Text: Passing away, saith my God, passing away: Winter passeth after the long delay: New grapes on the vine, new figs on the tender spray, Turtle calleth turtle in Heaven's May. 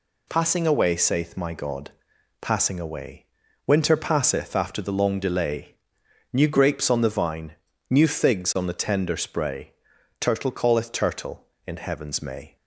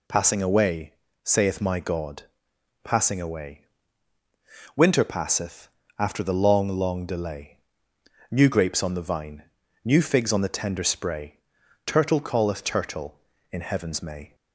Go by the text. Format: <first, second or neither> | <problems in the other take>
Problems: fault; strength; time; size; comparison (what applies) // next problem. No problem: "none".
first | pauses between "passeth" and "after"; slight; at 5.6 s; 0.32 s long // says "long" twice; at 6.6 s